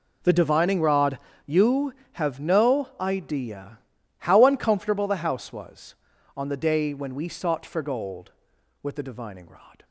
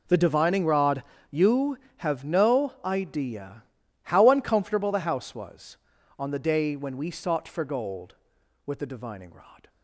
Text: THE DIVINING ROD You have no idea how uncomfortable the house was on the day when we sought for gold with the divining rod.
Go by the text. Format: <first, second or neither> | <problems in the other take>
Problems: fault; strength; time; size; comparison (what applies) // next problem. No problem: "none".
neither | pauses between "ROD" and "You"; slight; the same in both // pauses between "idea" and "how"; the same in both